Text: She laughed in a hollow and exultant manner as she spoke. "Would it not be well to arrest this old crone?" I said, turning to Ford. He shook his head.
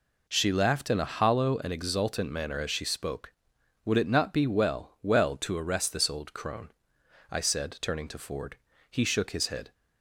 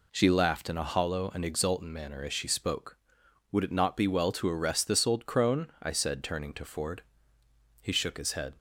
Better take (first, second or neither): second